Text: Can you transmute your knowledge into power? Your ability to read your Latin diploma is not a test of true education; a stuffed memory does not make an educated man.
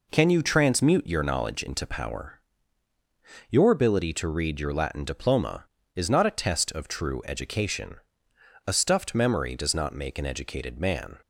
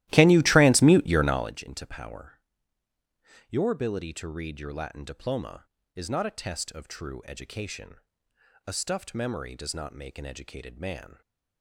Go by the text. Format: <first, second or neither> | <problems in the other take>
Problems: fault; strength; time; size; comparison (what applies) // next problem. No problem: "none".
first | starts louder than the rest; strong; until 1.5 s; 15.5 dB